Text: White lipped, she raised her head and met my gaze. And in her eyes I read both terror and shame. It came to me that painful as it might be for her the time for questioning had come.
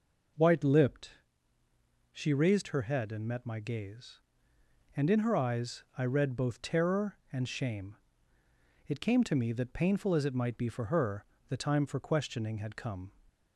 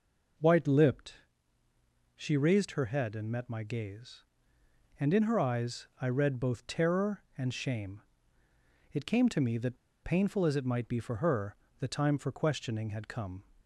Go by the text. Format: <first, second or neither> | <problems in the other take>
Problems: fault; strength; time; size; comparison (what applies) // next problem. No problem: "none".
first | pauses between "that" and "painful"; slight; at 9.7 s; 0.27 s long // pauses between "her" and "the"; slight; at 11.5 s; 0.24 s long; slight in the first